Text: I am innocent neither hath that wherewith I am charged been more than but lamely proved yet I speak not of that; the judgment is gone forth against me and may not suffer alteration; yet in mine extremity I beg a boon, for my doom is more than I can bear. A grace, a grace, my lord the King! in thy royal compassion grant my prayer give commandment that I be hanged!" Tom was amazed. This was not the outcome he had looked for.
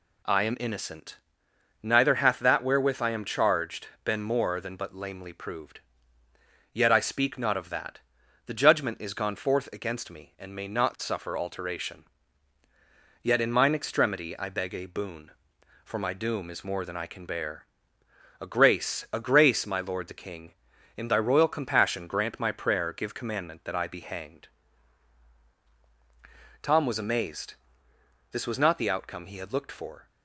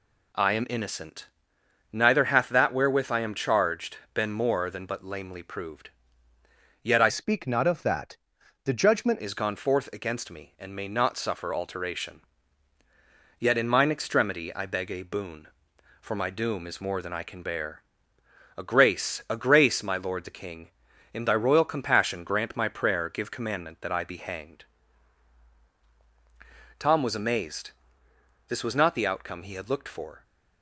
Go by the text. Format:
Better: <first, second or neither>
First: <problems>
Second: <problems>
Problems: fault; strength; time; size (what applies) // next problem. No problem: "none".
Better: first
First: pauses between "innocent" and "neither"; noticeable; at 1.1 s; 0.66 s long // pauses between "charged" and "been"; slight; at 3.8 s; 0.18 s long // pauses between "proved" and "yet"; noticeable; at 5.8 s; 0.92 s long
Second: pauses between "innocent" and "neither"; noticeable; at 1.2 s; 0.66 s long // pauses between "charged" and "been"; slight; at 3.9 s; 0.18 s long // pauses between "proved" and "yet"; noticeable; at 5.9 s; 0.92 s long // changes voice from "speak" to "judgment"; from 7.0 to 9.1 s; 2.1 s long